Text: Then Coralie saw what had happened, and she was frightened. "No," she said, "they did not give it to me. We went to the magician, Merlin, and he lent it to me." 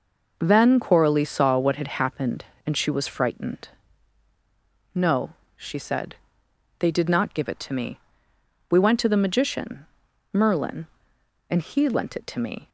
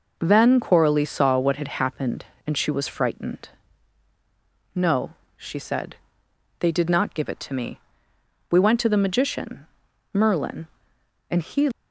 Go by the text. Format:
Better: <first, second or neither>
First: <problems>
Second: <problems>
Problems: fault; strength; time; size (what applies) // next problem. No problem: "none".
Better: first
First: none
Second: stops before "lent it to me"; at 11.7 s